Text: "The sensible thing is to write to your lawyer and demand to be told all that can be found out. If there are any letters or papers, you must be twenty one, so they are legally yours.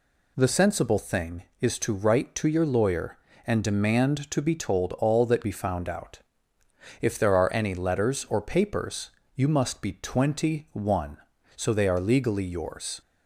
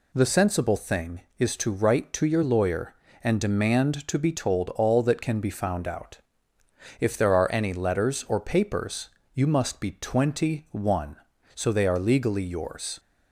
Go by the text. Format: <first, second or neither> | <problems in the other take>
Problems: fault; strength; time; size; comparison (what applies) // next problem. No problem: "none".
second | skips "can"; at 5.4 s